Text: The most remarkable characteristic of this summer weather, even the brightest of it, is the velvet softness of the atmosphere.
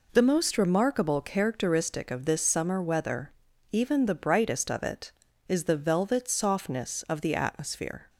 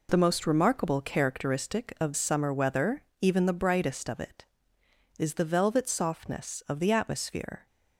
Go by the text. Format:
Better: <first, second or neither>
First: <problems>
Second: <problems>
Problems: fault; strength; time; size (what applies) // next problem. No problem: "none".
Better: first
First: none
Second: skips "this"; at 2.1 s